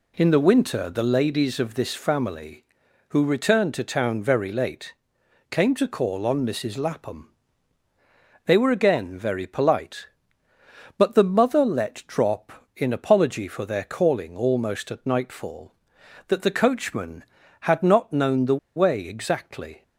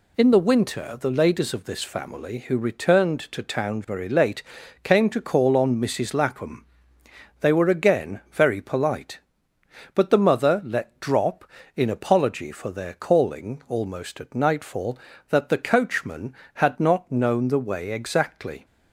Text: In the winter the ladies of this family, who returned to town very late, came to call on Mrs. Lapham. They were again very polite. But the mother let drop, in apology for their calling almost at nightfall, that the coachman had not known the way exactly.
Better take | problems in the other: second | pauses between "the" and "way"; slight; at 18.5 s; 0.19 s long

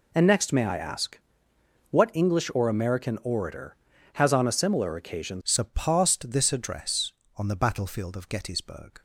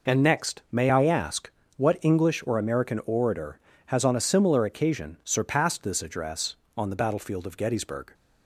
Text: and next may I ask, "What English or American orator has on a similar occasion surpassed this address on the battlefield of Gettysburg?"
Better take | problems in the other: second | changes voice at "surpassed"; from 5.4 s on; 3.6 s long

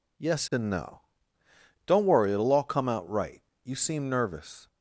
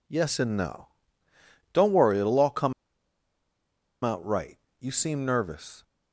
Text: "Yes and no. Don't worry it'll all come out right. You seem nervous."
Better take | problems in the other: first | pauses between "come" and "out"; strong; at 2.7 s; 1.3 s long

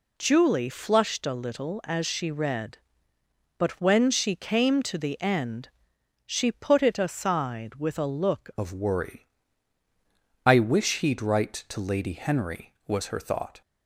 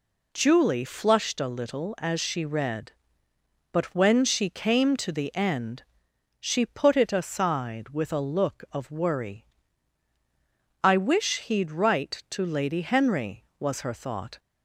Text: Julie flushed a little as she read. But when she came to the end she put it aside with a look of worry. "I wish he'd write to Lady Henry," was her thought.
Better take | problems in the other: second | pauses between "end" and "she"; noticeable; at 5.6 s; 0.58 s long; noticeable in the second // changes voice at "of"; from 8.5 s on; 5.1 s long

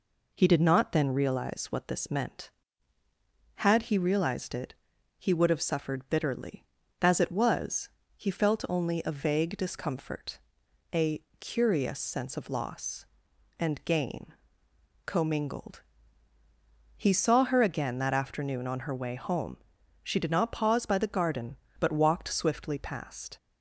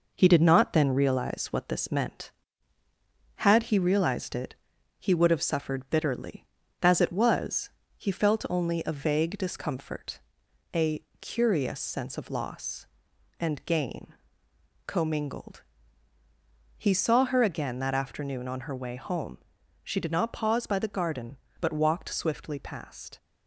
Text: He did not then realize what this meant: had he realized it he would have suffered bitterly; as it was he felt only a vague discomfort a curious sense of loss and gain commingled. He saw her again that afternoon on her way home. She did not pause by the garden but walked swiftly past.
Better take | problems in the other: first | gets quieter; throughout; 3.5 dB // pauses between "it" and "he"; noticeable; at 4.5 s; 0.46 s long; noticeable in the first // pauses between "was" and "he"; slight; at 7.7 s; 0.26 s long; slight in the first // pauses between "discomfort" and "a"; noticeable; at 10.1 s; 0.52 s long; noticeable in the first // pauses between "a" and "curious"; slight; at 11.0 s; 0.16 s long; slight in the first // pauses between "gain" and "commingled"; noticeable; at 14.1 s; 0.72 s long; noticeable in the first

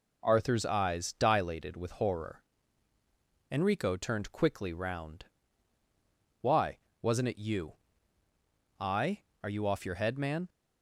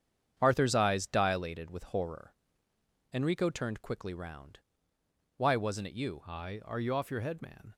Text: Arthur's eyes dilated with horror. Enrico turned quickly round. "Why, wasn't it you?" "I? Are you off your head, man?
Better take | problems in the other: first | gets quieter; strong; throughout; 7.5 dB

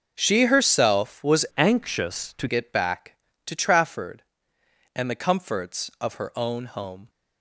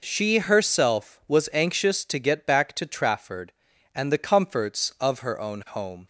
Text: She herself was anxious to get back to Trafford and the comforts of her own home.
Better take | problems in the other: second | changes voice from "anxious" to "to"; from 1.5 to 2.4 s; 0.9 s long

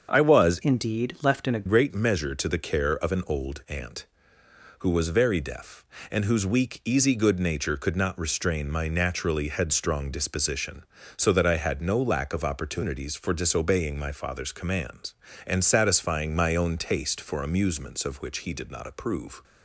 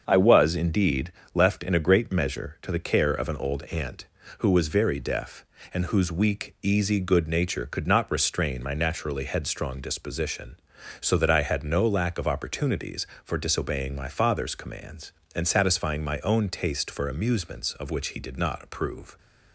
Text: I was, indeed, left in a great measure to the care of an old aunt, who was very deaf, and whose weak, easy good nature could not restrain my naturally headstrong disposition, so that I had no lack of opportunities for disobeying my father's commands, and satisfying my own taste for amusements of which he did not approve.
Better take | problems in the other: second | starts louder than the rest; until 1.1 s; 7 dB; also in the second // changes voice from "indeed" to "a"; from 0.6 to 1.6 s; 1.0 s long

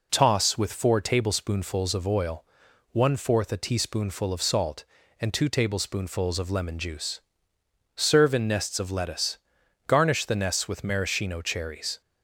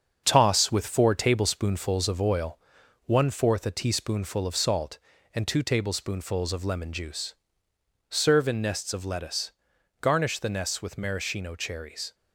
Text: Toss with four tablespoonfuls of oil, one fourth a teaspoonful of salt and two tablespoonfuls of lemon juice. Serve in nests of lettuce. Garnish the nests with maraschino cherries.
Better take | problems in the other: first | gets quieter; noticeable; throughout; 6 dB

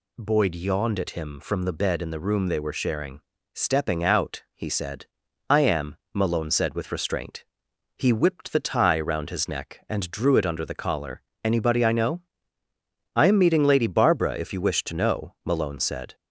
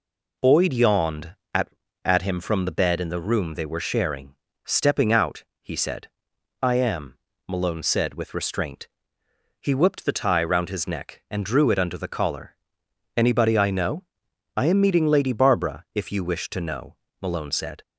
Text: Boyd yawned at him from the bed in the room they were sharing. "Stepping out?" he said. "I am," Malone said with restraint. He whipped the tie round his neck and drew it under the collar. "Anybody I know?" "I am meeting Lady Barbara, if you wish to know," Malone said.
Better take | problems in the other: first | says "at" twice; at 2.0 s

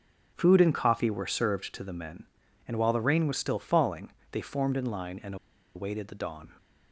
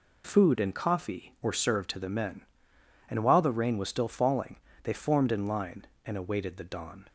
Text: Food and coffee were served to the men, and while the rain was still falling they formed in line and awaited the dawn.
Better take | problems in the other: second | starts louder than the rest; strong; until 1.3 s; 8 dB // pauses between "falling" and "they"; slight; at 4.0 s; 0.22 s long; slight in the second // pauses between "and" and "awaited"; at 5.3 s; 0.39 s long

